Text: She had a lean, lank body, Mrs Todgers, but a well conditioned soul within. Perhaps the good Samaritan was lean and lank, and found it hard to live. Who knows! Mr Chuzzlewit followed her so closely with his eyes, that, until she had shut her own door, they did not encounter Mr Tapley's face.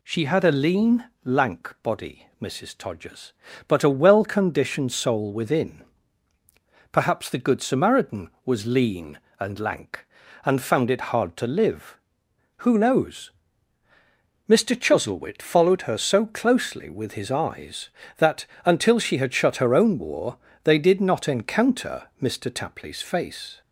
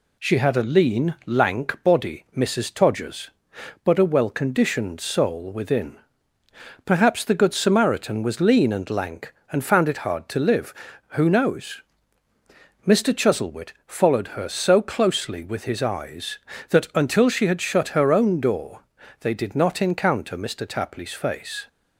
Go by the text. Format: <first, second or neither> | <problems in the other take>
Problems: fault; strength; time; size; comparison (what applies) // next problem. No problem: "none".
second | says "war" for "door"; at 19.9 s